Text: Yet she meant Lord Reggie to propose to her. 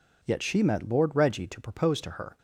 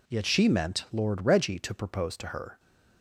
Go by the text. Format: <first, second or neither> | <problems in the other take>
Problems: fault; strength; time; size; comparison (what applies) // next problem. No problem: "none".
second | says "met" for "meant"; at 0.6 s